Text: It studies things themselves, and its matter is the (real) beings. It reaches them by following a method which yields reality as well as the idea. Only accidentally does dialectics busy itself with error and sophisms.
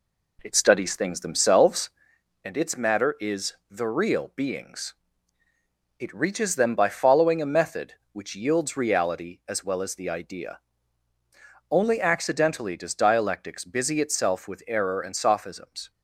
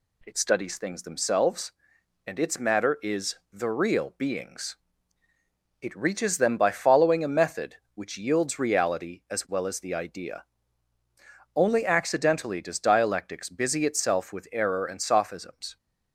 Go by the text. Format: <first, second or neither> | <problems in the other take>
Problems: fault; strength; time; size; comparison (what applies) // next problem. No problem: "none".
second | starts louder than the rest; slight; until 2.1 s; 3 dB